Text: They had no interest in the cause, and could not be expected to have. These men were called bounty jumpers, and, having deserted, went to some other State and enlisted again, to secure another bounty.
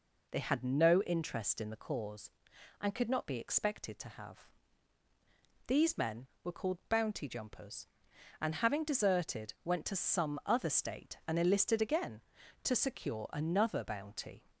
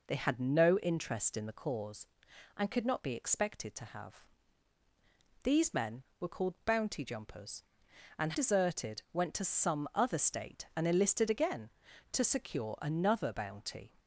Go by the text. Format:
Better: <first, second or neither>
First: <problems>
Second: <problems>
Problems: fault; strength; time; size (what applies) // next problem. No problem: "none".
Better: first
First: none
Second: skips "having"; at 8.3 s